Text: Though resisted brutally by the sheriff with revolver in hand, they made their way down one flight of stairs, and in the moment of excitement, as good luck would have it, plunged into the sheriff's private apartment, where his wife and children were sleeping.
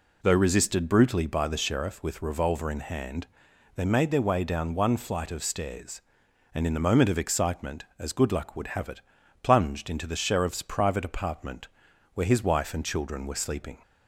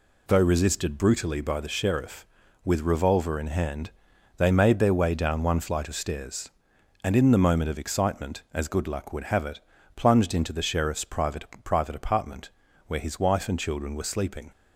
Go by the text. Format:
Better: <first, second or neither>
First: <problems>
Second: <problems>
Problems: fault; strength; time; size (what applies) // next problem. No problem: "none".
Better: first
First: none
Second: says "private" twice; at 11.6 s